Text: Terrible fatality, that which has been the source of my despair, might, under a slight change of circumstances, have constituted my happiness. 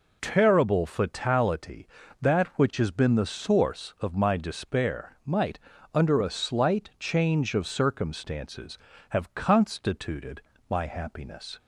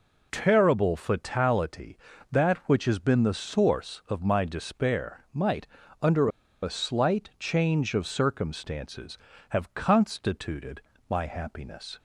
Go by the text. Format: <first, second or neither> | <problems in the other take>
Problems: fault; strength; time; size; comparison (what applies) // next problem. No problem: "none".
first | pauses between "under" and "a"; slight; at 6.2 s; 0.34 s long // pauses between "constituted" and "my"; slight; at 10.7 s; 0.28 s long; slight in the first